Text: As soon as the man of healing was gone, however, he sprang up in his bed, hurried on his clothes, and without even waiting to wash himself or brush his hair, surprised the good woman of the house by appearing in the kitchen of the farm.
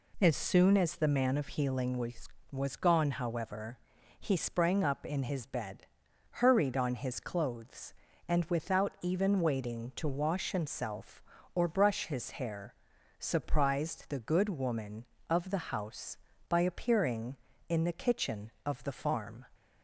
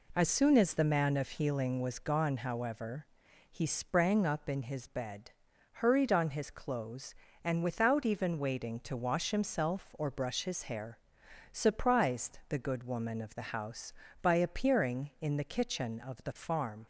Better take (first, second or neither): second